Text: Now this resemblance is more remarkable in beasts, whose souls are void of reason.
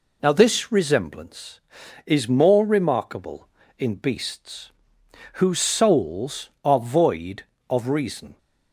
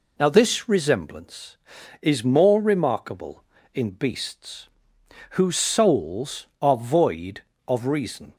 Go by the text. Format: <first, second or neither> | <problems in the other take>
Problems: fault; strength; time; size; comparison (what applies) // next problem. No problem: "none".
neither | none